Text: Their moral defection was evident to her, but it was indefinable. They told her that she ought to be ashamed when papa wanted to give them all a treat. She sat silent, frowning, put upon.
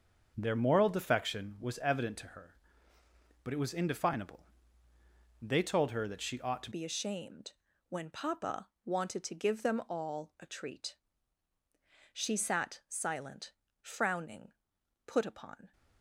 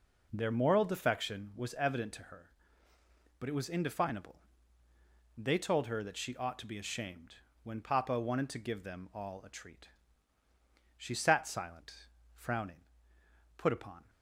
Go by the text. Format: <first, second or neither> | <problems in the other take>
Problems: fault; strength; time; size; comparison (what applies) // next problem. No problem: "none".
second | starts louder than the rest; until 1.3 s; 6.5 dB // changes voice at "be"; from 6.7 s on; 9.0 s long // pauses between "ashamed" and "when"; slight; at 7.5 s; 0.34 s long; slight in the second // pauses between "papa" and "wanted"; slight; at 8.6 s; 0.16 s long